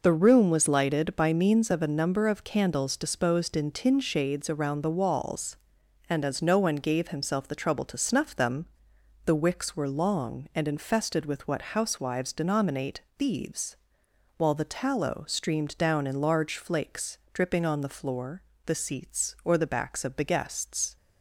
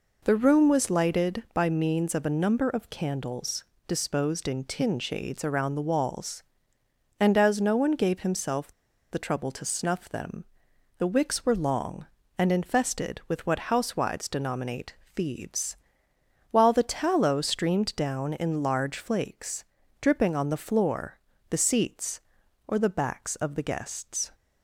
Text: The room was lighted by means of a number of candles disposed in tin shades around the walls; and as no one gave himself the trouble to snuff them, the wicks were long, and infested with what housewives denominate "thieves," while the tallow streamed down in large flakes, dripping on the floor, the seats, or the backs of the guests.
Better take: first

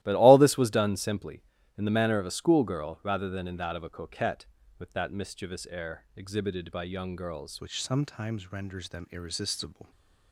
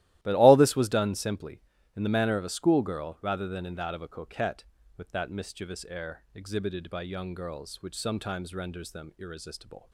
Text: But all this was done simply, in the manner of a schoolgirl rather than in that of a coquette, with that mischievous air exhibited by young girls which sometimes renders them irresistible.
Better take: second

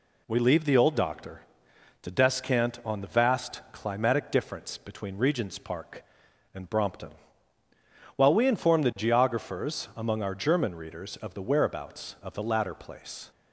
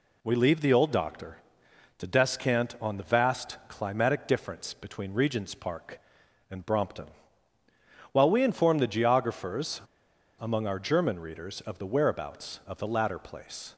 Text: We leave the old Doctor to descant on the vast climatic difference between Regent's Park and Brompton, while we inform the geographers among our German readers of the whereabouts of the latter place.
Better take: first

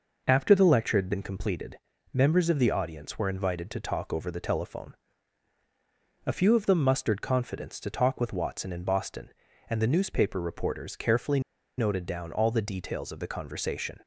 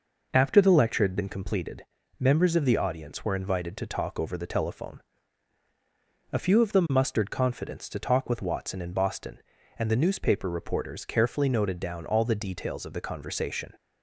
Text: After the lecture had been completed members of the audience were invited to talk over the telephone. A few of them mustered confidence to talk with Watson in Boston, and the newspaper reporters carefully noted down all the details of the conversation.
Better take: second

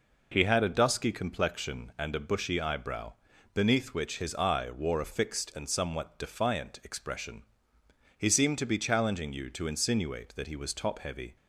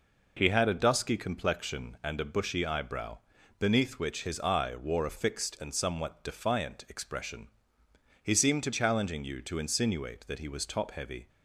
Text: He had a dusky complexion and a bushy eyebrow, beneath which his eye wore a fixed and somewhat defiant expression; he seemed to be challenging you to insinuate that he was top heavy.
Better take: first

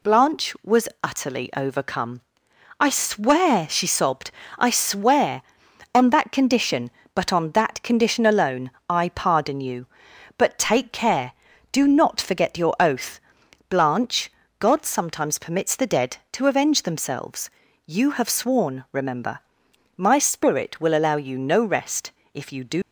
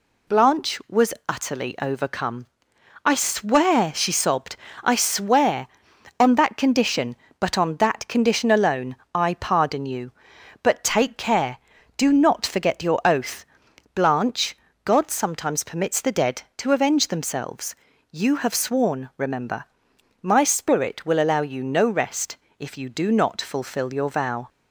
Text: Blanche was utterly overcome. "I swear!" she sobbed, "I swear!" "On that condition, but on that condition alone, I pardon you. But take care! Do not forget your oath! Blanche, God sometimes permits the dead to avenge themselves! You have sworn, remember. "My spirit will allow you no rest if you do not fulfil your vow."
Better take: second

